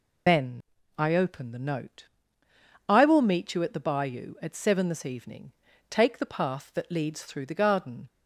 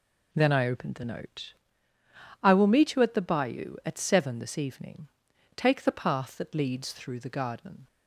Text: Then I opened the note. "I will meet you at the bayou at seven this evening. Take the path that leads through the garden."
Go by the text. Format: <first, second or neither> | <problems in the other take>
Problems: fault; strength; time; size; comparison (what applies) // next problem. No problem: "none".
second | loses the start of "Then"; at 0.2 s; 140 ms // pauses between "Then" and "I"; slight; at 0.6 s; 0.36 s long